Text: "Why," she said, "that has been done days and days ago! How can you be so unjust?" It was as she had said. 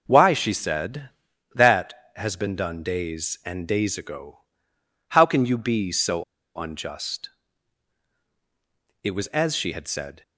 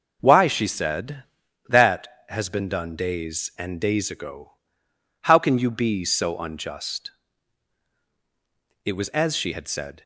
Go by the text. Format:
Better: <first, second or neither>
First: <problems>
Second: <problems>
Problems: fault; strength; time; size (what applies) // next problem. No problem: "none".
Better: second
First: pauses between "so" and "unjust"; slight; at 6.2 s; 0.32 s long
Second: none